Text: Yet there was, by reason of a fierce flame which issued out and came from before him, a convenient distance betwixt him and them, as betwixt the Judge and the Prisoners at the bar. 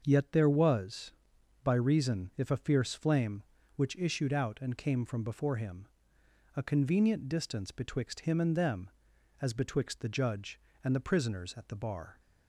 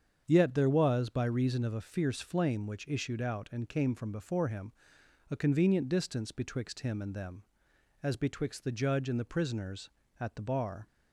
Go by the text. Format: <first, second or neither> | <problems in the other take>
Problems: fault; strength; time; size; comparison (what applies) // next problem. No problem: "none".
second | starts louder than the rest; until 1.0 s; 6.5 dB; strong in the second // says "if" for "of"; at 2.3 s